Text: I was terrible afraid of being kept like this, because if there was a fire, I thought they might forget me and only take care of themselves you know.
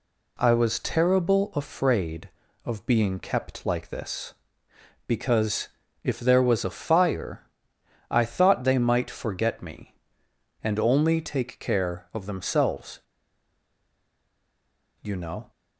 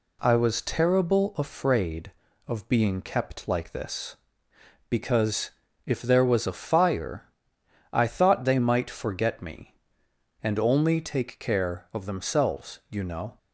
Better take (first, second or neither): second